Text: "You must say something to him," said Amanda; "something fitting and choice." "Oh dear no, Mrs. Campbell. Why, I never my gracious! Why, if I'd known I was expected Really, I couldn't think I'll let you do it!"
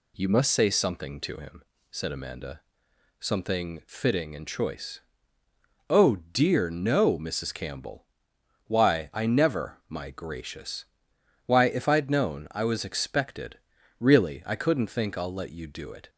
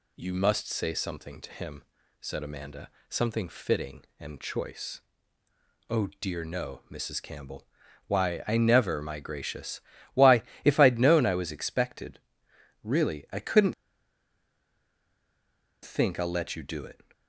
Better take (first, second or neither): first